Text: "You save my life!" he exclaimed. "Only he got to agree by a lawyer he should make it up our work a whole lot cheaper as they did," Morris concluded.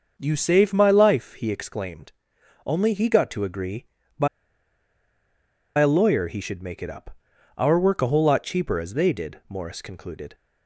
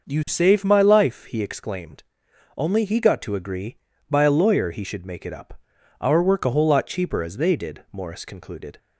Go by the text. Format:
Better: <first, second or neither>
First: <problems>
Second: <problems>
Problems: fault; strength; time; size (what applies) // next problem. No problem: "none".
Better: second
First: starts louder than the rest; until 1.1 s; 6.5 dB // pauses between "by" and "a"; strong; at 4.2 s; 1.5 s long // pauses between "up" and "our"; at 7.1 s; 0.40 s long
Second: starts louder than the rest; noticeable; until 1.1 s; 6 dB // pauses between "up" and "our"; at 5.5 s; 0.40 s long